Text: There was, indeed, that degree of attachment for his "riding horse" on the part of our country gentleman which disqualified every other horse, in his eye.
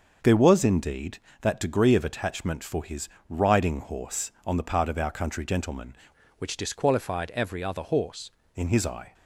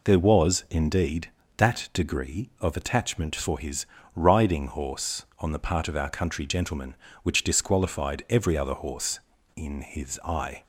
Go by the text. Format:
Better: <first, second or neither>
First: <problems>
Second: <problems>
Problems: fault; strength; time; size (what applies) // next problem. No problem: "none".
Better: second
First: starts louder than the rest; until 1.4 s; 6 dB // pauses between "his" and "riding"; slight; at 3.0 s; 0.22 s long // changes voice from "which" to "horse"; from 6.3 to 8.3 s; 2.0 s long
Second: pauses between "his" and "riding"; slight; at 3.8 s; 0.30 s long